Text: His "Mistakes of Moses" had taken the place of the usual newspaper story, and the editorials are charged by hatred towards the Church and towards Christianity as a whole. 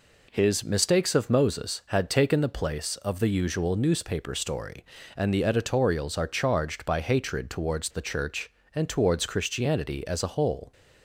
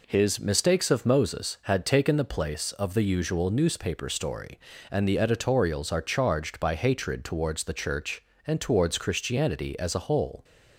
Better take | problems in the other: neither | none

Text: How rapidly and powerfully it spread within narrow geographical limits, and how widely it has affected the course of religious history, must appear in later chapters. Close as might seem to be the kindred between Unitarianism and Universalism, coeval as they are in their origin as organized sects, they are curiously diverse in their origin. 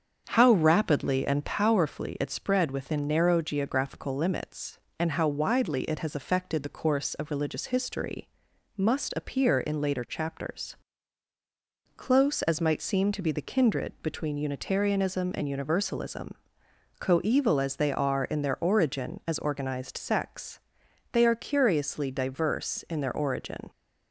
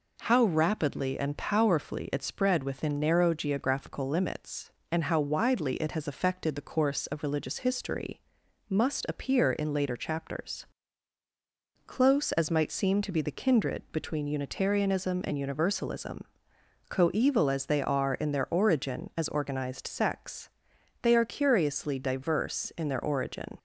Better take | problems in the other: second | starts louder than the rest; strong; until 1.7 s; 7.5 dB

